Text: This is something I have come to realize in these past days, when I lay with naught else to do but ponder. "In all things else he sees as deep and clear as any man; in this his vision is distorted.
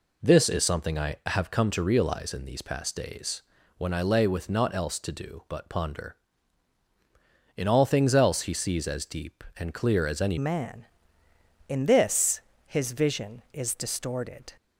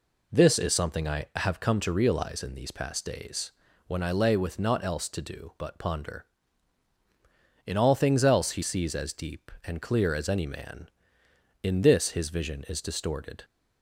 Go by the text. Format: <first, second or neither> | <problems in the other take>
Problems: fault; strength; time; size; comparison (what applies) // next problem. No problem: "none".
second | changes voice at "man"; from 10.3 s on; 4.2 s long // pauses between "this" and "his"; slight; at 12.3 s; 0.28 s long